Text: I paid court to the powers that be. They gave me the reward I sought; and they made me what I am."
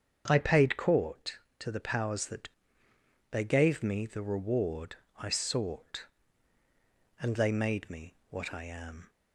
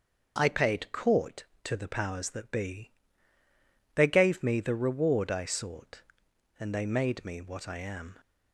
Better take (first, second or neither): second